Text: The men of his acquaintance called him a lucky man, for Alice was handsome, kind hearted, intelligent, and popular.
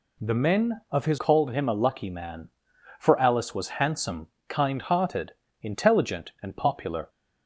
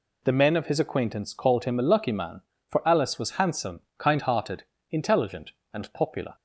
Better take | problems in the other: second | skips "acquaintance"; at 1.1 s

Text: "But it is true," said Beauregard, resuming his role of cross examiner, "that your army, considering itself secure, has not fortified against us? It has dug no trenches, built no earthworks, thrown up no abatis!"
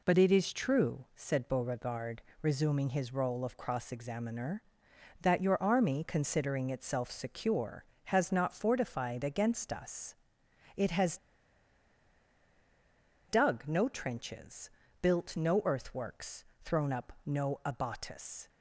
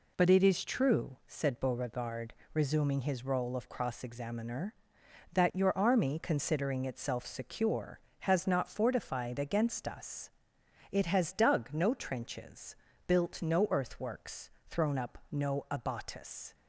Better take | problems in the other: second | pauses between "has" and "dug"; strong; at 11.1 s; 2.1 s long

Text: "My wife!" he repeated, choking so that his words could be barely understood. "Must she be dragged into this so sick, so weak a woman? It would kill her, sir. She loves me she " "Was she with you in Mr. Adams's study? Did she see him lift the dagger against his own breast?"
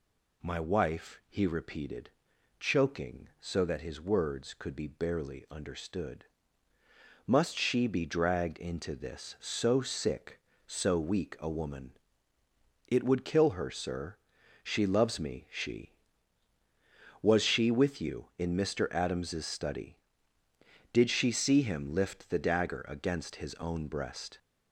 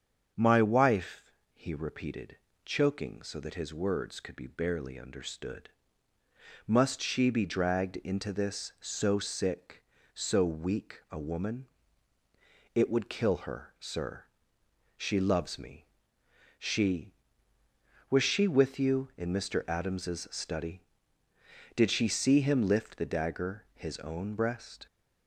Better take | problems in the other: first | starts louder than the rest; strong; until 1.5 s; 7.5 dB // pauses between "me" and "she"; noticeable; at 15.8 s; 0.74 s long // skips "against"; at 23.7 s

